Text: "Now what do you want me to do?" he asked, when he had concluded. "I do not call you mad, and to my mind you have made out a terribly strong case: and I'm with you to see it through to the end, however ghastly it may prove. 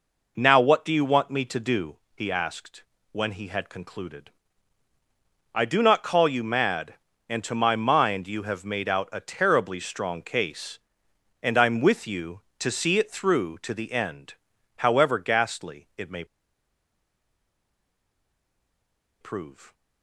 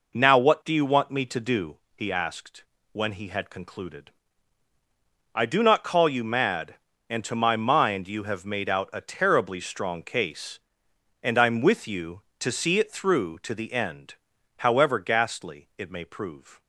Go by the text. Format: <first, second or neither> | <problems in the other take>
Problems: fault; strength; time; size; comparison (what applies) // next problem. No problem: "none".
second | pauses between "may" and "prove"; strong; at 16.2 s; 2.9 s long